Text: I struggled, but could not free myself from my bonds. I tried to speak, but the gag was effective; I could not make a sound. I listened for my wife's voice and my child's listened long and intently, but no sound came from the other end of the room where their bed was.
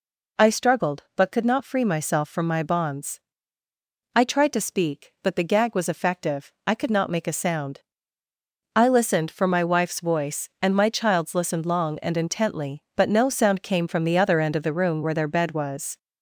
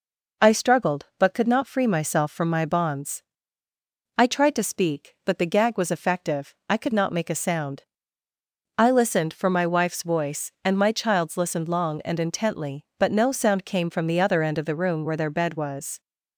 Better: second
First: gets louder; throughout; 3.5 dB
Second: none

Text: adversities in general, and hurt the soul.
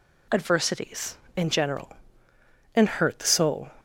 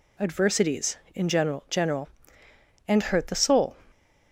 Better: first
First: none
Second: says "general" twice; at 1.6 s

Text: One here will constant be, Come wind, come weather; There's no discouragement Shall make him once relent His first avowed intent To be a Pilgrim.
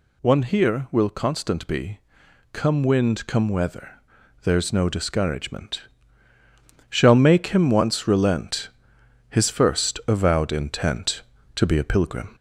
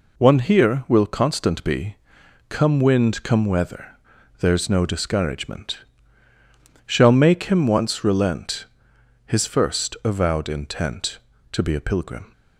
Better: second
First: gets louder; slight; throughout; 2.5 dB // pauses between "discouragement" and "Shall"; at 5.8 s; 1.0 s long // pauses between "relent" and "His"; noticeable; at 8.6 s; 0.62 s long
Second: pauses between "discouragement" and "Shall"; at 5.7 s; 1.0 s long // pauses between "relent" and "His"; noticeable; at 8.6 s; 0.62 s long

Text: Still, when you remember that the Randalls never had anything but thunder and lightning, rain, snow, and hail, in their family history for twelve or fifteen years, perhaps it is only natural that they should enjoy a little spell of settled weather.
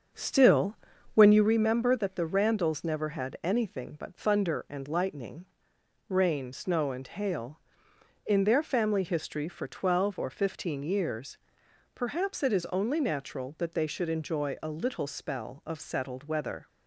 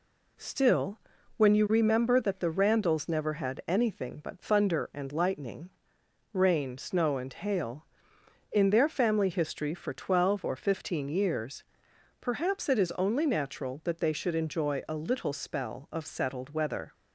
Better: second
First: starts louder than the rest; strong; until 1.5 s; 7 dB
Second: none

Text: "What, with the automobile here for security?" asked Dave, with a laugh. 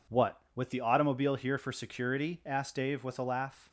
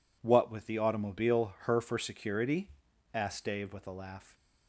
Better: first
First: none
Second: says "her" for "here"; at 1.6 s

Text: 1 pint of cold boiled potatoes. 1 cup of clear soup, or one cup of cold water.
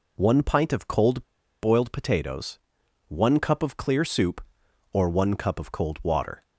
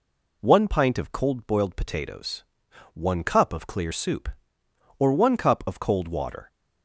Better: second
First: pauses between "cold" and "boiled"; at 1.2 s; 0.37 s long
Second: none

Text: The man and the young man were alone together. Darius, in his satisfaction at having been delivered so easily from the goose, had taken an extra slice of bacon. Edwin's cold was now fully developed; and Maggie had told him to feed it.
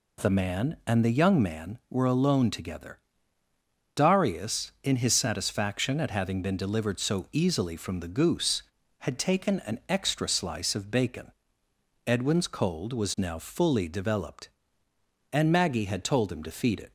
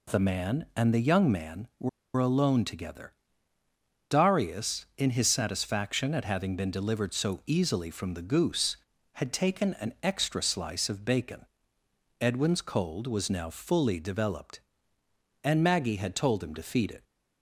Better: first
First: none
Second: pauses between "were" and "alone"; slight; at 1.8 s; 0.27 s long

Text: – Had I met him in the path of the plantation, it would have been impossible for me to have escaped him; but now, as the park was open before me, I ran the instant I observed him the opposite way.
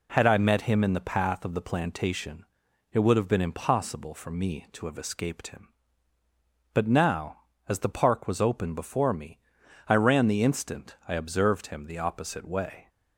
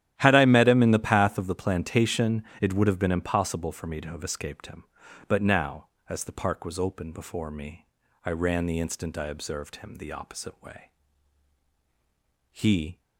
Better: first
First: none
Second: starts louder than the rest; strong; until 1.1 s; 12 dB // goes on to say "He"; slight; from 12.5 s on; 0.48 s long

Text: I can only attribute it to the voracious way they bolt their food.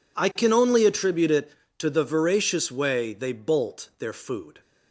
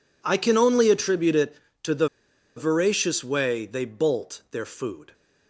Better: first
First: none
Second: pauses between "the" and "voracious"; noticeable; at 2.0 s; 0.49 s long

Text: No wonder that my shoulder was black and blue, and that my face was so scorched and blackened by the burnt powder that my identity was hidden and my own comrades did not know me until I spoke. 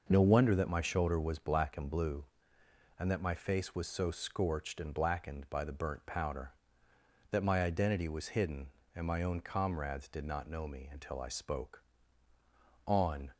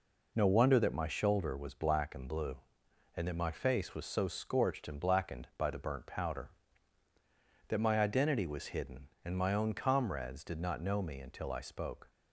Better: second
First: goes on to say "On"; slight; from 12.8 s on; 0.46 s long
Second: none

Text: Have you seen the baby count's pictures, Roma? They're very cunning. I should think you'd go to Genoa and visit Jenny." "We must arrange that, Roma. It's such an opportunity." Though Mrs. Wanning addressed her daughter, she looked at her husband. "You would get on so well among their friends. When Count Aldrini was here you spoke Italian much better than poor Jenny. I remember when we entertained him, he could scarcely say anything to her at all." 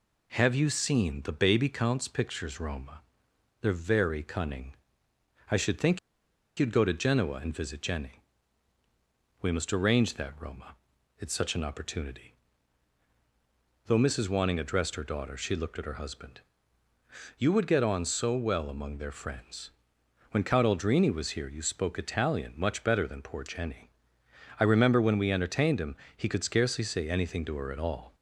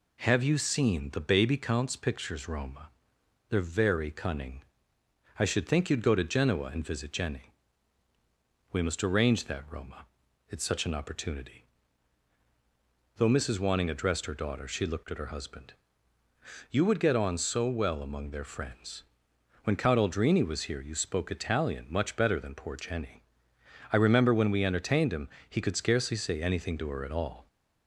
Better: second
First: pauses between "think" and "you'd"; noticeable; at 5.9 s; 0.59 s long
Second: none

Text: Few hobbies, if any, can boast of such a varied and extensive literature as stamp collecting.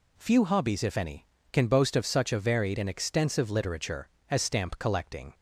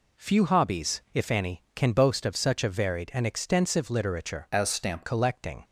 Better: first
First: none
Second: changes voice from "as" to "stamp"; from 4.5 to 5.0 s; 0.5 s long

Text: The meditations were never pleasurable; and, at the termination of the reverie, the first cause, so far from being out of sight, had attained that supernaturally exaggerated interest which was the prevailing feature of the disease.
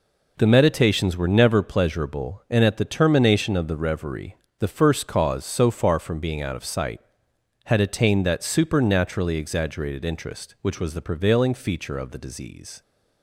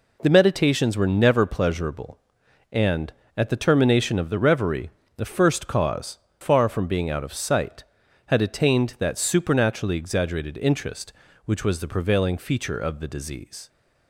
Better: first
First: none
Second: skips "so"; at 6.2 s

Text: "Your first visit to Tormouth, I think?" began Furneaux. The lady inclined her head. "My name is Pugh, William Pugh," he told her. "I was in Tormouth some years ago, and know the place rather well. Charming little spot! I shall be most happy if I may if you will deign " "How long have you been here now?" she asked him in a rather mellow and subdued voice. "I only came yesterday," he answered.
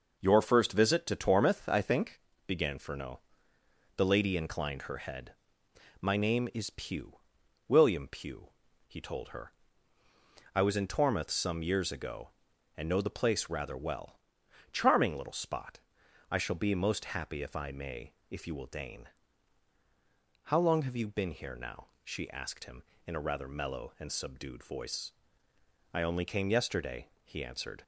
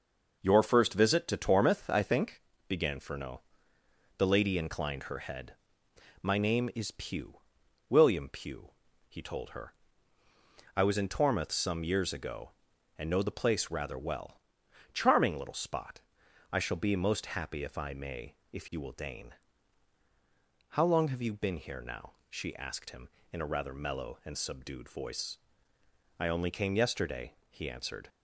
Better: neither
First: pauses between "may" and "if"; slight; at 18.1 s; 0.18 s long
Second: pauses between "may" and "if"; slight; at 18.3 s; 0.18 s long

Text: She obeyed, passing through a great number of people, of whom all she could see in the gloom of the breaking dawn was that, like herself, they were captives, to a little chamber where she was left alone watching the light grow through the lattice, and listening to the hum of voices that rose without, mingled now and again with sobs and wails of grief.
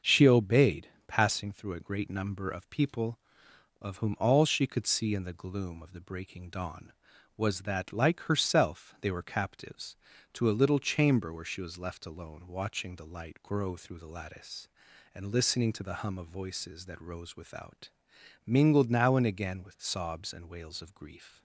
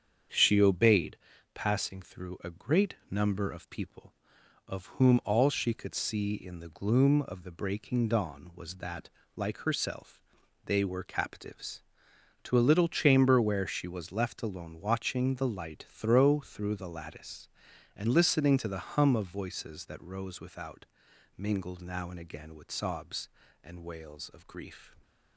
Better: first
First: starts louder than the rest; until 1.2 s; 6.5 dB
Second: starts louder than the rest; strong; until 1.7 s; 7.5 dB // pauses between "great" and "number"; slight; at 2.9 s; 0.16 s long // says "throw" for "grow"; at 15.8 s

